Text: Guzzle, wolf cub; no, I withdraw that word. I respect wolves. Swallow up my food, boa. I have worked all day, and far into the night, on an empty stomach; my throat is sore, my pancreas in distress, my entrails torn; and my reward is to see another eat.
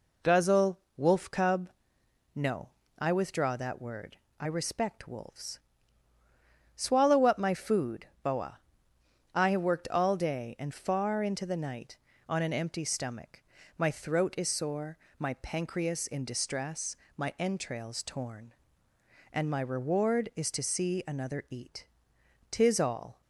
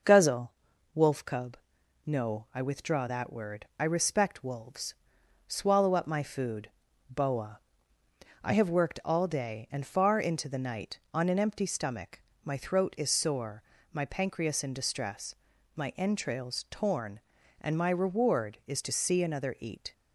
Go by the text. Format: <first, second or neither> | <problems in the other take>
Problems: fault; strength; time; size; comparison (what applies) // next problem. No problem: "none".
second | goes on to say "Tis all"; noticeable; from 22.5 s on; 0.70 s long